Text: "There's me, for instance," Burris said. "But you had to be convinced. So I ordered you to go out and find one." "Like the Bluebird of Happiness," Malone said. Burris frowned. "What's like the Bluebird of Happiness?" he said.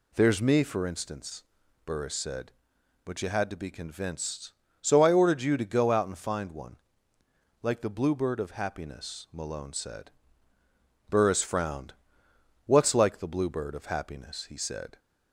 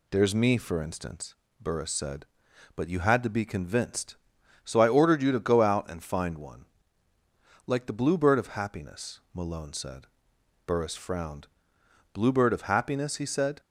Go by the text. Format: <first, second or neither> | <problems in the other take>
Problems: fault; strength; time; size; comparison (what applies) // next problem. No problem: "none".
first | skips "What's like the"; at 11.8 s